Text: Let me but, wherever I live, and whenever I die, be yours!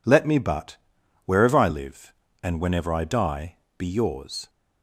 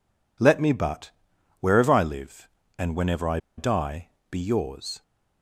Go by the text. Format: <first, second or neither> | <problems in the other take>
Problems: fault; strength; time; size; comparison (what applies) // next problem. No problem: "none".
first | pauses between "I" and "die"; slight; at 3.3 s; 0.18 s long